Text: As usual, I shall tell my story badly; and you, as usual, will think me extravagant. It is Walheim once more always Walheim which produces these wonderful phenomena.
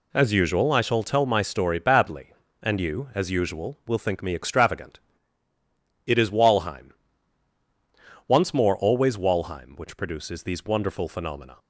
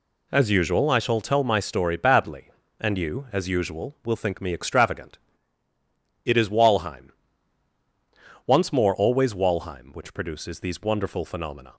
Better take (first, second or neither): neither